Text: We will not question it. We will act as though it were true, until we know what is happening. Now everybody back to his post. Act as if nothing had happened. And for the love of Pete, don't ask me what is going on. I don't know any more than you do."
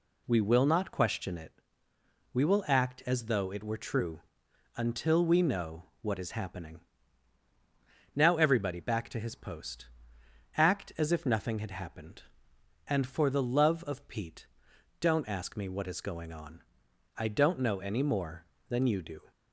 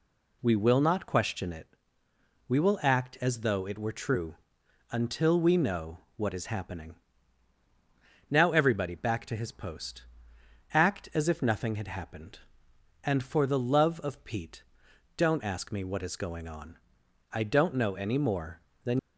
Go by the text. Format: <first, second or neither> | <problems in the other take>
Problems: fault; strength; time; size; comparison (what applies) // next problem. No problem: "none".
first | pauses between "know" and "what"; slight; at 6.0 s; 0.16 s long; slight in the first // stops before "you do"; at 18.9 s